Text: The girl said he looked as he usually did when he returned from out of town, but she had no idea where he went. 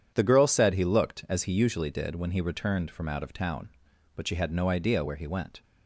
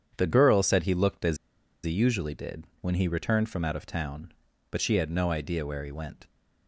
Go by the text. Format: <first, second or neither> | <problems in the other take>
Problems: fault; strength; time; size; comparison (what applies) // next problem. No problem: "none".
first | starts louder than the rest; strong; until 1.1 s; 8 dB // pauses between "as" and "he"; noticeable; at 1.3 s; 0.48 s long // pauses between "did" and "when"; slight; at 2.6 s; 0.16 s long